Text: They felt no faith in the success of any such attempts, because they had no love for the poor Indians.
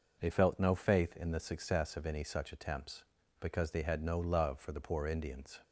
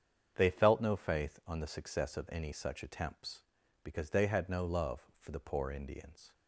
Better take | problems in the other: first | starts louder than the rest; strong; until 1.3 s; 7.5 dB // says "on" for "in"; at 1.4 s

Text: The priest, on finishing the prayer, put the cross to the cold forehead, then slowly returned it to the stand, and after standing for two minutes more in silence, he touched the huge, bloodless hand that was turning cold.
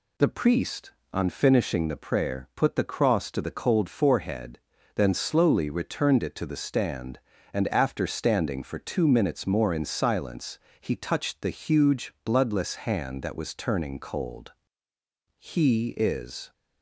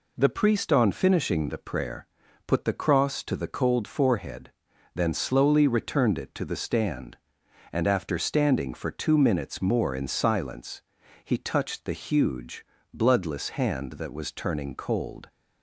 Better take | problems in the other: second | goes on to say "He is"; noticeable; from 15.3 s on; 1.1 s long

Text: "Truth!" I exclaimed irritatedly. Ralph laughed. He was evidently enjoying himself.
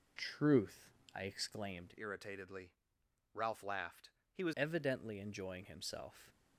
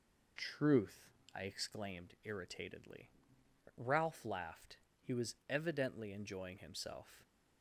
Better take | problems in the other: second | changes voice from "irritatedly" to "was"; from 1.9 to 4.5 s; 2.6 s long

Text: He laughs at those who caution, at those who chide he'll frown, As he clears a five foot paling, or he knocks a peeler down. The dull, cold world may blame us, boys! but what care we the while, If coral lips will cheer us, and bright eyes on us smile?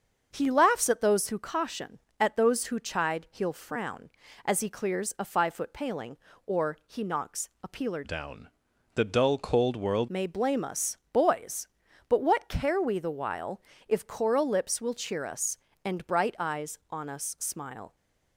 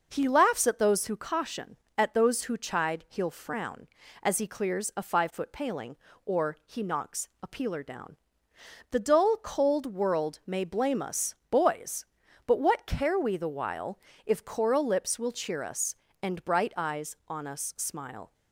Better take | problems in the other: second | starts louder than the rest; until 1.3 s; 7 dB // changes voice from "down" to "world"; from 8.0 to 10.0 s; 2.0 s long

